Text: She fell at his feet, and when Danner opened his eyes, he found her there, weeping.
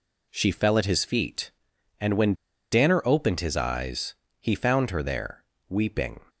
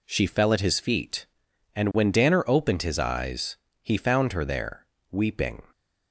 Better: second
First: pauses between "when" and "Danner"; at 2.3 s; 0.37 s long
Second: none

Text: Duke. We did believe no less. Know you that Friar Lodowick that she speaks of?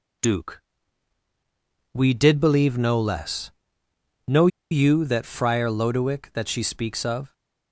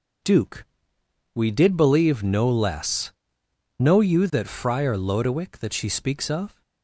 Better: second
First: pauses between "Know" and "you"; slight; at 4.4 s; 0.23 s long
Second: none

